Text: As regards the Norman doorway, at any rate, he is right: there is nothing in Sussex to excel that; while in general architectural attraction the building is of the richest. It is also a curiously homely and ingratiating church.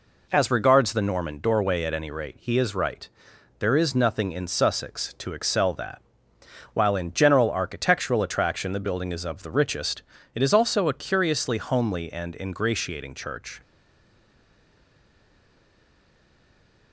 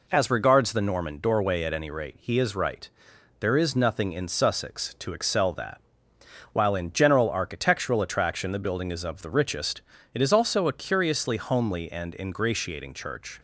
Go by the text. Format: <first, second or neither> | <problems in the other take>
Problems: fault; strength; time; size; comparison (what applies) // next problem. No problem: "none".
second | stays silent after the last word; strong; from 13.6 s on; 3.3 s long